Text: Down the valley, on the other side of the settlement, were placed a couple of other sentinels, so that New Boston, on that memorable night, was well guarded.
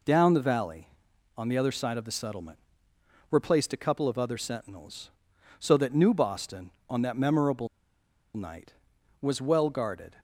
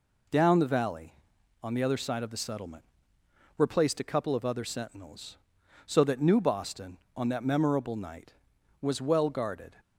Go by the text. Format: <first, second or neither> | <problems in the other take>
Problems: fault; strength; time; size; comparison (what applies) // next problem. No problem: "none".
second | pauses between "memorable" and "night"; noticeable; at 7.6 s; 0.69 s long